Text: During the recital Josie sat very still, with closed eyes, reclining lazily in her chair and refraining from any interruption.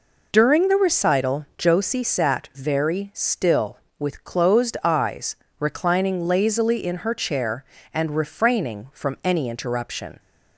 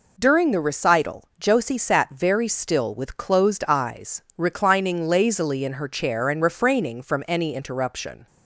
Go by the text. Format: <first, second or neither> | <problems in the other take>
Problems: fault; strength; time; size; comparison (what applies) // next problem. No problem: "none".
neither | none